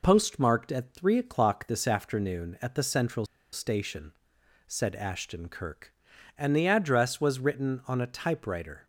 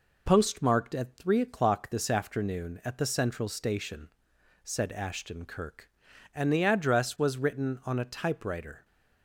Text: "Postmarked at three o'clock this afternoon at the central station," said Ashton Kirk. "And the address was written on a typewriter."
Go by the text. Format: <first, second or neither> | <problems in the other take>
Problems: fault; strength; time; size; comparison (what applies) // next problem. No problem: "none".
second | pauses between "central" and "station"; slight; at 3.2 s; 0.28 s long